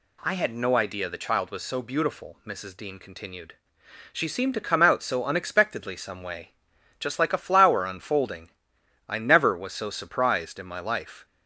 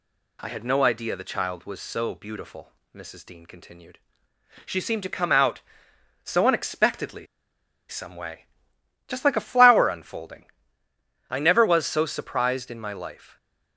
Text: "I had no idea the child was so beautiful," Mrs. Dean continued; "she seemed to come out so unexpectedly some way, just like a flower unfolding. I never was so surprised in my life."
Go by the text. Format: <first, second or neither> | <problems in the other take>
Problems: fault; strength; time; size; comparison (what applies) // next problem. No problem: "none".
first | pauses between "unexpectedly" and "some"; noticeable; at 7.2 s; 0.62 s long